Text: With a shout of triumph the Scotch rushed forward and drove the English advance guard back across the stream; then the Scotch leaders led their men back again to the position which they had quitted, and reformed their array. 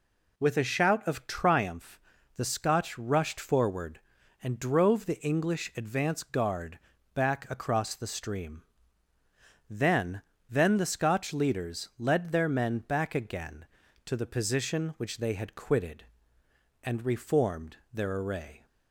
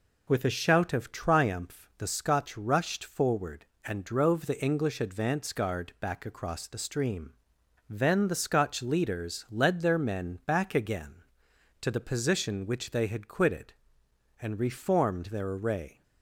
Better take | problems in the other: second | pauses between "triumph" and "the"; at 1.9 s; 0.38 s long // pauses between "guard" and "back"; slight; at 6.7 s; 0.36 s long // says "then" twice; at 10.4 s // pauses between "reformed" and "their"; slight; at 17.7 s; 0.16 s long

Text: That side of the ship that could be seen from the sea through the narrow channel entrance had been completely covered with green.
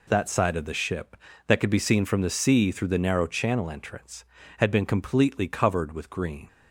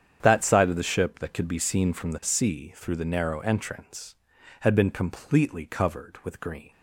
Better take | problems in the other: first | starts louder than the rest; strong; until 1.2 s; 8.5 dB // skips "channel"; at 3.4 s

